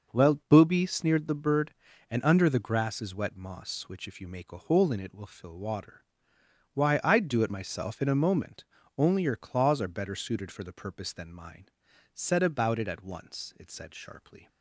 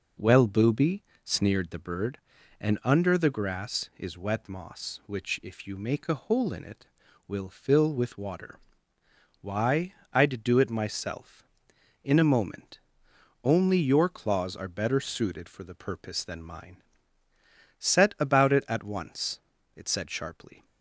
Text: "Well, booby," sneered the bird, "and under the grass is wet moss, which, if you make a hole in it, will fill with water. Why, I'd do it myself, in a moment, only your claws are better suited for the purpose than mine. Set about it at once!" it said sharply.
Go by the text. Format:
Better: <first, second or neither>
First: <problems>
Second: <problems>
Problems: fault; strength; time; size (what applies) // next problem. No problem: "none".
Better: second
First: skips "with"; at 5.5 s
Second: none